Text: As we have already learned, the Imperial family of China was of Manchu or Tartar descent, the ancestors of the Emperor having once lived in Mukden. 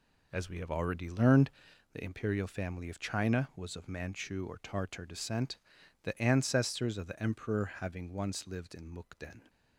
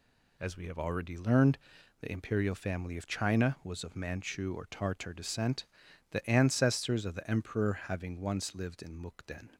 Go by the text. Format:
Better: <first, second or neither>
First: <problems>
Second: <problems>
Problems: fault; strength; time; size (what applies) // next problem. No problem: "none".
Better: second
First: starts louder than the rest; until 1.7 s; 4 dB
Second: none